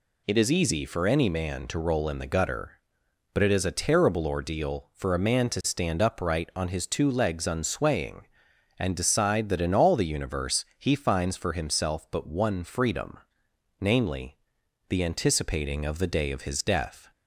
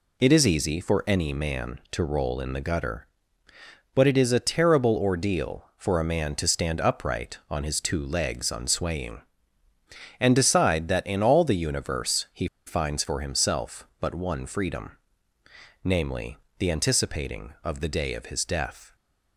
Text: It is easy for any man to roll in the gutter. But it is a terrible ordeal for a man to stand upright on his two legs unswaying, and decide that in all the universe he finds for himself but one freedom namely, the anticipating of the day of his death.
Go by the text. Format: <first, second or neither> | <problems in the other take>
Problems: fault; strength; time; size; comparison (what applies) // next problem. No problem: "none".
first | pauses between "he" and "finds"; slight; at 12.4 s; 0.19 s long // pauses between "freedom" and "namely"; noticeable; at 14.9 s; 0.96 s long; noticeable in the first